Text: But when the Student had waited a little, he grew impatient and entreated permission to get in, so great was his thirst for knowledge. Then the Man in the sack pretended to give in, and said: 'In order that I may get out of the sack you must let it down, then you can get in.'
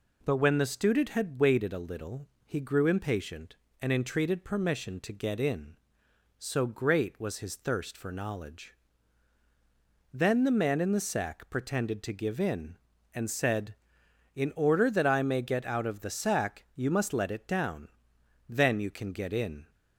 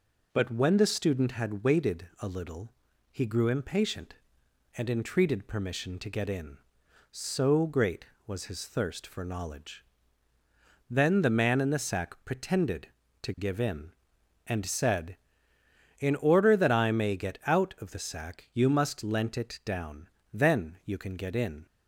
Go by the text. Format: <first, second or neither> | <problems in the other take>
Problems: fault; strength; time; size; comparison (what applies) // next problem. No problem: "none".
first | says "lent" for "let"; at 19.0 s